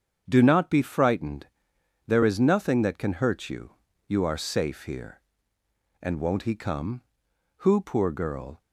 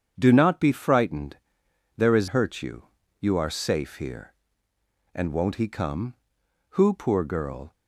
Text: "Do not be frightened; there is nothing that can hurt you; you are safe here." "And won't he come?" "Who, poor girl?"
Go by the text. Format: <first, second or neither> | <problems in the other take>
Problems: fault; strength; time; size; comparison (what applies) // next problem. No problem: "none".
first | starts louder than the rest; strong; until 1.1 s; 7.5 dB; strong in the first // skips "nothing that can"; at 2.2 s